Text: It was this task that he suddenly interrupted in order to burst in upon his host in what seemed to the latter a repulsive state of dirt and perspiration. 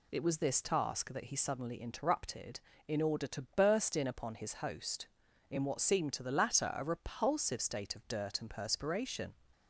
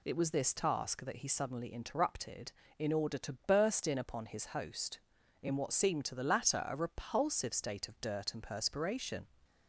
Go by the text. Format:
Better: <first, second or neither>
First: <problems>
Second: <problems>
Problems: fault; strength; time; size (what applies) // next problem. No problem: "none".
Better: neither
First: none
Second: none